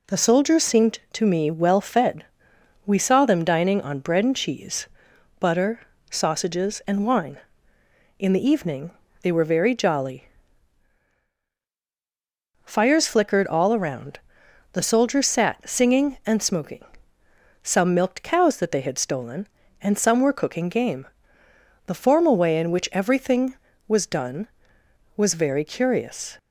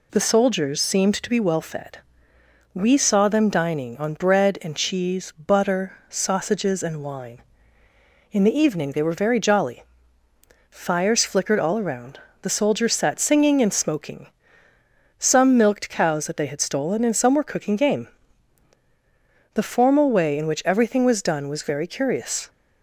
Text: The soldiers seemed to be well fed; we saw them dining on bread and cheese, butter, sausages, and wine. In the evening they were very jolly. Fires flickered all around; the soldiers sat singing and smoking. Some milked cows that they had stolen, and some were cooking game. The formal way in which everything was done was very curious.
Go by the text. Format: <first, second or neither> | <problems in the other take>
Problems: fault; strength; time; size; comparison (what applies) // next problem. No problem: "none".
second | says "me" for "be"; at 1.2 s // pauses between "evening" and "they"; slight; at 8.9 s; 0.32 s long